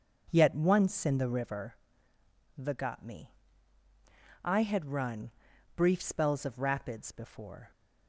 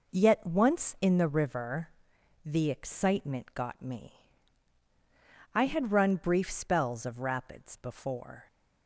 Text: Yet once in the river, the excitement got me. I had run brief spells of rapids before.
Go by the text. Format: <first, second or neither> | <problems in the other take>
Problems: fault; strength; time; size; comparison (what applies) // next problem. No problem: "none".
second | skips "excitement"; at 2.7 s // pauses between "run" and "brief"; at 5.3 s; 0.44 s long